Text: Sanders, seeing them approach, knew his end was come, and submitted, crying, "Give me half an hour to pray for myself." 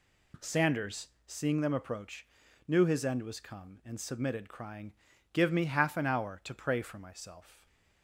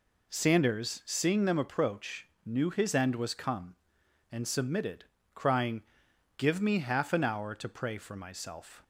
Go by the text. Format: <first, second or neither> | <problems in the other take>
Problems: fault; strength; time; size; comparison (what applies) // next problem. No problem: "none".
neither | none